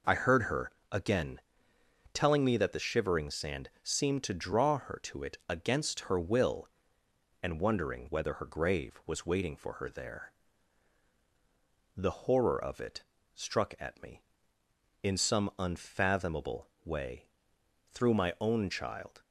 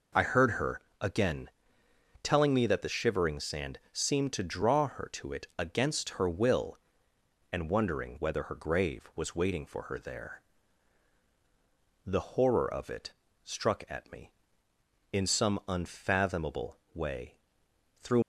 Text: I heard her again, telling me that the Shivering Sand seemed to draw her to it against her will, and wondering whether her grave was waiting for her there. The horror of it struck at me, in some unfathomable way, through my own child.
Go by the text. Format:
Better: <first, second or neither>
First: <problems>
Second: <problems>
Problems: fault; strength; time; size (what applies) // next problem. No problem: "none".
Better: first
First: pauses between "her" and "again"; slight; at 0.7 s; 0.22 s long // pauses between "it" and "struck"; slight; at 13.0 s; 0.32 s long // pauses between "unfathomable" and "way"; slight; at 16.6 s; 0.16 s long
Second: pauses between "her" and "again"; slight; at 0.7 s; 0.22 s long // pauses between "it" and "struck"; slight; at 13.1 s; 0.32 s long // pauses between "unfathomable" and "way"; slight; at 16.7 s; 0.16 s long // stops before "my own child"; at 18.2 s